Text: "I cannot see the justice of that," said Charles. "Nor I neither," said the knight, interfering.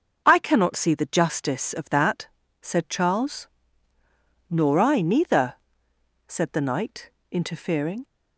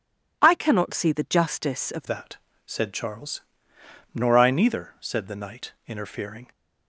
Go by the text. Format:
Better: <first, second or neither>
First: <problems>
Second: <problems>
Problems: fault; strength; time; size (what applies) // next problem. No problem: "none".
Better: first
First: none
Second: changes voice at "that"; from 2.0 s on; 4.4 s long